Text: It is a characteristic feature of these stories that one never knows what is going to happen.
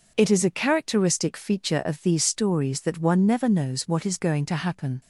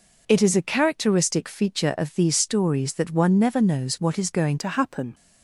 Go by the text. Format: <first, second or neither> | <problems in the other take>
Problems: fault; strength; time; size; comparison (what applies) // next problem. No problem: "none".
first | changes voice at "to"; from 4.5 s on; 0.6 s long